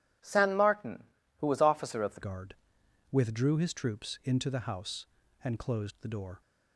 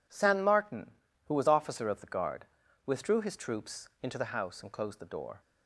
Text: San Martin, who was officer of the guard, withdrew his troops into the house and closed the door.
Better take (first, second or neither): second